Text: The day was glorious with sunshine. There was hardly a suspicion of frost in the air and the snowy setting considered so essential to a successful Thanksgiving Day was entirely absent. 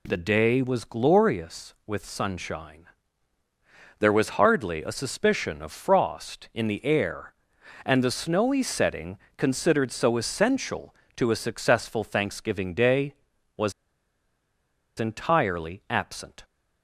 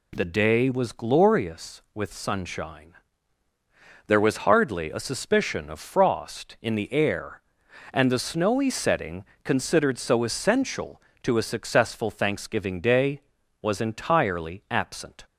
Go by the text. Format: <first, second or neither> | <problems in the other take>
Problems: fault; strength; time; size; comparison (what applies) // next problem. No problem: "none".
second | pauses between "setting" and "considered"; slight; at 9.1 s; 0.18 s long; slight in the second // pauses between "was" and "entirely"; strong; at 13.7 s; 1.2 s long